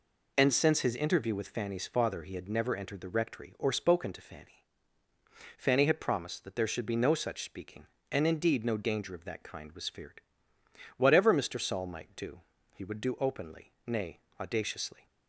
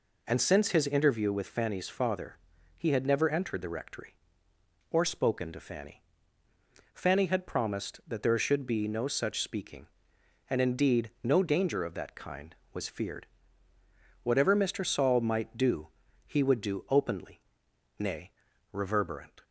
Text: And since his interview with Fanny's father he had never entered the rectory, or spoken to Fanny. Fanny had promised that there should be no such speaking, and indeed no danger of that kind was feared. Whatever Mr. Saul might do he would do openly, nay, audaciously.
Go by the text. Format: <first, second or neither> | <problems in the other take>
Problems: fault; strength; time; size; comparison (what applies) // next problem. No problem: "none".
first | pauses between "father" and "he"; at 2.3 s; 0.40 s long // pauses between "do" and "he"; at 15.8 s; 0.40 s long; slight in the first // says "reverberant" for "audaciously"; at 18.7 s